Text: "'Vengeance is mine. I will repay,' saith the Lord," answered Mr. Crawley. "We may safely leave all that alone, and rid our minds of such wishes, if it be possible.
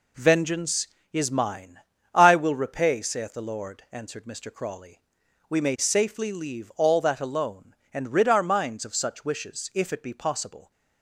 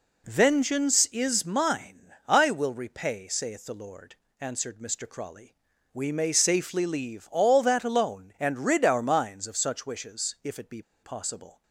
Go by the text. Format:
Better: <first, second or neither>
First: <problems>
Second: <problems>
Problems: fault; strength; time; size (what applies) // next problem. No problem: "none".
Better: first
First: none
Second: pauses between "be" and "possible"; slight; at 10.8 s; 0.21 s long